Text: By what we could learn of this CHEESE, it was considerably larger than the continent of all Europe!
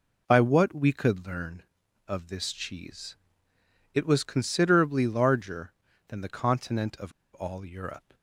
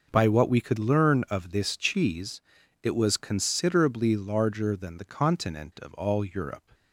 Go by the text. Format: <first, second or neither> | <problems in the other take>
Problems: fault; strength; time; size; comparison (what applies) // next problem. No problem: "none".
second | pauses between "of" and "all"; slight; at 7.1 s; 0.23 s long